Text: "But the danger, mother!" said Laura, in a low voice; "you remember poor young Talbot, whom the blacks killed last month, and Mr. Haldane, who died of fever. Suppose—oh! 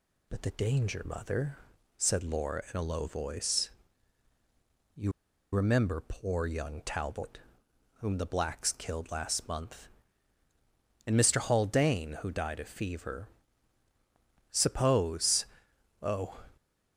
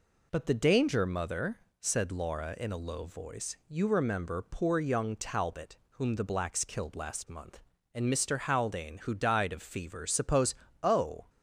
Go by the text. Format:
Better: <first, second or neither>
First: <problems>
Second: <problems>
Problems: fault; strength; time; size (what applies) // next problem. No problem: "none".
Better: second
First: pauses between "you" and "remember"; at 5.0 s; 0.44 s long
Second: none